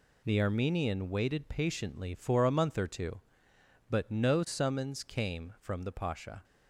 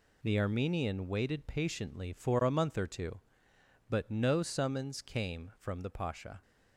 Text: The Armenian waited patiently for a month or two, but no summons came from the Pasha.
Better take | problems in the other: neither | none

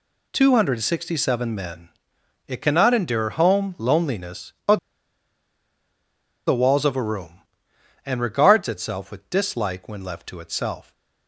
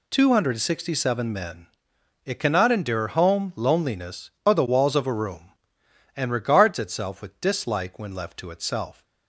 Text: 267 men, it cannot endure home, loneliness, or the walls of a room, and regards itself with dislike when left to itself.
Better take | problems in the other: second | pauses between "or" and "the"; strong; at 4.7 s; 1.7 s long

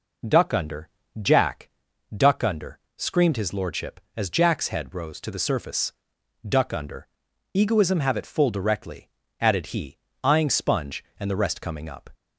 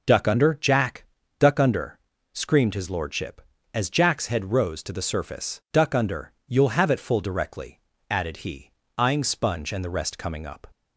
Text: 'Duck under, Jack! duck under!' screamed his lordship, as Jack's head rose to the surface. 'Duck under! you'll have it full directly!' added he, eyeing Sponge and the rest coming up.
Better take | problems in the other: second | says "egoism" for "you'll"; at 7.5 s

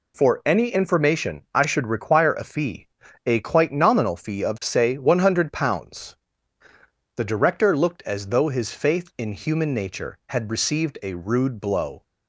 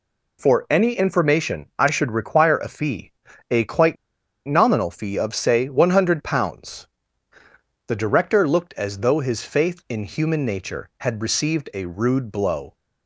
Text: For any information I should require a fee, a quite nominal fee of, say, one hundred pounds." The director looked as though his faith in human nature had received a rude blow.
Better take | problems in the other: first | pauses between "quite" and "nominal"; noticeable; at 3.9 s; 0.52 s long

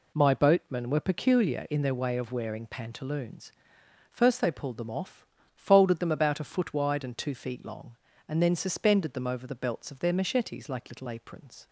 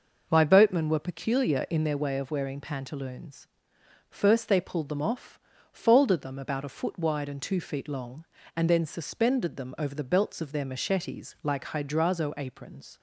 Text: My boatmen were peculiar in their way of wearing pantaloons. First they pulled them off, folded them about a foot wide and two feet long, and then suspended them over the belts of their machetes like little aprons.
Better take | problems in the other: first | says "hydrazo" for "little"; at 11.6 s

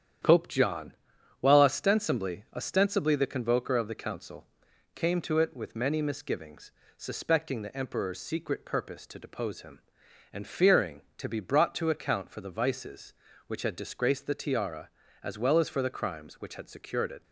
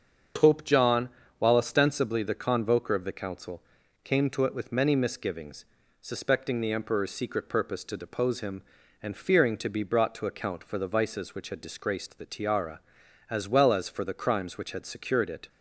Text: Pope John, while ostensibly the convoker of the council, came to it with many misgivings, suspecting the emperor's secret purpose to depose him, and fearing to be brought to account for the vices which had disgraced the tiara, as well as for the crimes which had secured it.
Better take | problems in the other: second | starts louder than the rest; strong; until 1.7 s; 10 dB; also in the second // says "ostensibly" twice; at 2.5 s

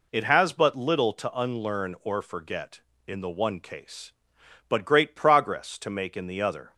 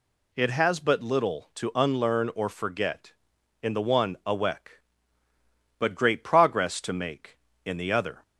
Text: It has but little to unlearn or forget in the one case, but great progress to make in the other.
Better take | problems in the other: first | says "awek" for "case"; at 4.2 s

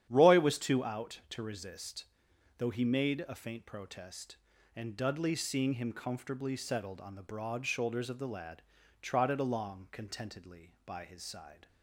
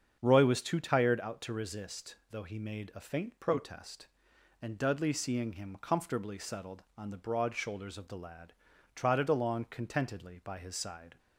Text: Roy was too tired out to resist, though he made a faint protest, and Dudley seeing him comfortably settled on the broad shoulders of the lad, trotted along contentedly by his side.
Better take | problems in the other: second | starts louder than the rest; strong; until 1.1 s; 10 dB; strong in the second // skips "tired"; at 0.8 s

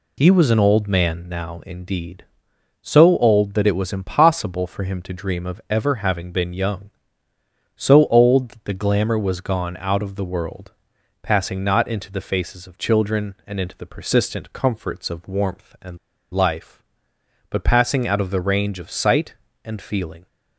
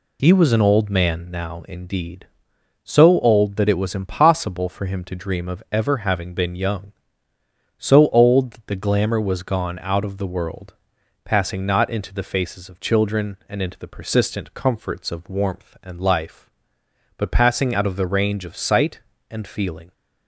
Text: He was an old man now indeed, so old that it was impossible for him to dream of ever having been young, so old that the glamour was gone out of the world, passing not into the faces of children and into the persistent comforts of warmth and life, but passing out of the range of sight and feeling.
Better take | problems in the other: second | pauses between "and" and "life"; at 15.9 s; 0.37 s long

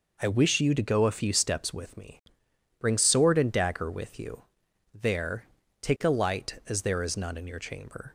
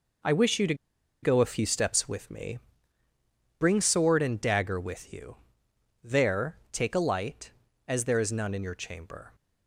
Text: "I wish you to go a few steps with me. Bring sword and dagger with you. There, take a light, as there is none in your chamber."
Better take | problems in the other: first | pauses between "to" and "go"; noticeable; at 0.7 s; 0.48 s long

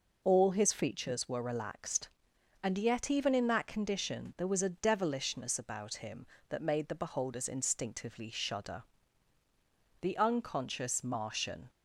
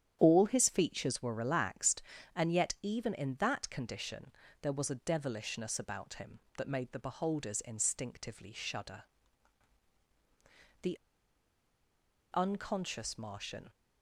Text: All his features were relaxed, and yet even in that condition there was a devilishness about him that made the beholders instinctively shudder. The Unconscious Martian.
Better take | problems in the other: first | starts louder than the rest; strong; until 1.2 s; 10 dB // pauses between "condition" and "there"; slight; at 4.3 s; 0.28 s long // pauses between "The" and "Unconscious"; strong; at 10.9 s; 1.3 s long

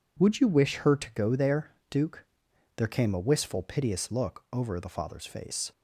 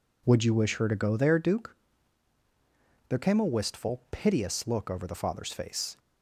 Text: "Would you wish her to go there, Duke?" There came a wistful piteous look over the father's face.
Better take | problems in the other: neither | none

